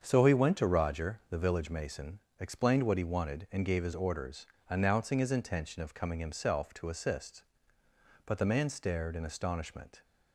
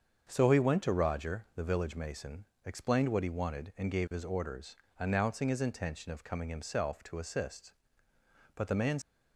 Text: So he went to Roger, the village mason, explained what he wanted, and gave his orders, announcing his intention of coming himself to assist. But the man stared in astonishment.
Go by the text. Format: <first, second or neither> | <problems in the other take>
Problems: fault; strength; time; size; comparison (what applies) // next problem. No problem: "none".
first | starts louder than the rest; until 1.3 s; 7 dB; strong in the first // stops before "stared in astonishment"; at 9.0 s